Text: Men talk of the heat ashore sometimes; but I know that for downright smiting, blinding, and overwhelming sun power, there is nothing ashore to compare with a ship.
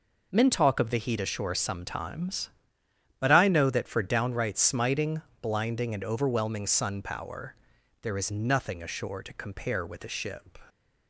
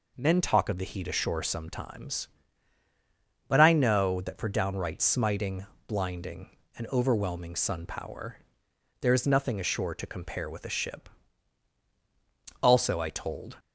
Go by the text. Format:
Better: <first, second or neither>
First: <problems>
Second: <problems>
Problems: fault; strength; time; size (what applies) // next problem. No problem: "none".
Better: first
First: none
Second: goes on to say "Also I told"; noticeable; from 12.6 s on; 0.96 s long